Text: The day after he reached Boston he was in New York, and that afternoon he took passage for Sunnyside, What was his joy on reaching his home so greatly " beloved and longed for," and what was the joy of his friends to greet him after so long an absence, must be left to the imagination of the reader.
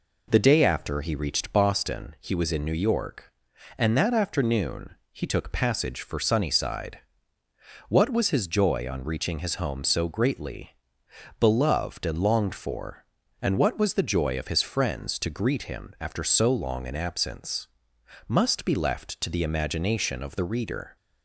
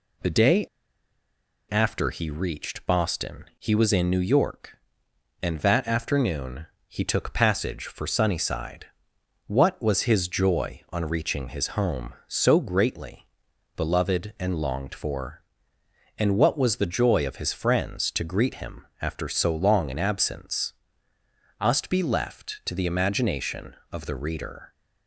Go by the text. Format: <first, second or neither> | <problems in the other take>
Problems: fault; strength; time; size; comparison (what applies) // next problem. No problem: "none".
first | pauses between "day" and "after"; at 0.6 s; 1.0 s long // pauses between "afternoon" and "he"; slight; at 6.6 s; 0.20 s long; slight in the first // pauses between "him" and "after"; slight; at 18.8 s; 0.16 s long